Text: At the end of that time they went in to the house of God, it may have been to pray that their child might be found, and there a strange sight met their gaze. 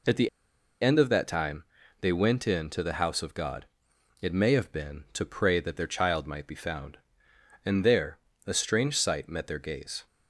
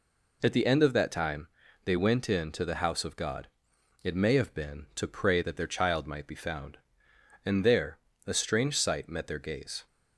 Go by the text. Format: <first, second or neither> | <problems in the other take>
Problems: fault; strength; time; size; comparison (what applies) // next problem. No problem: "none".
second | pauses between "the" and "end"; noticeable; at 0.2 s; 0.53 s long // pauses between "time" and "they"; slight; at 1.6 s; 0.36 s long; slight in the second // pauses between "there" and "a"; slight; at 8.1 s; 0.30 s long; slight in the second